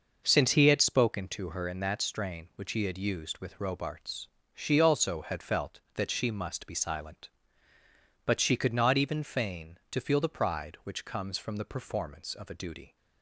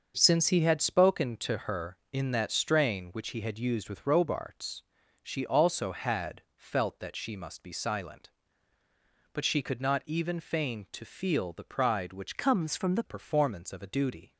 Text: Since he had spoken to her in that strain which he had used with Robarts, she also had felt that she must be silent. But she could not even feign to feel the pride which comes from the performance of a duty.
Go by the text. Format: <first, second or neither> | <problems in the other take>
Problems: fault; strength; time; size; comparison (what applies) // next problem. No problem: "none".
first | starts louder than the rest; noticeable; until 1.1 s; 6 dB // changes voice from "comes" to "the"; from 12.3 to 13.0 s; 0.7 s long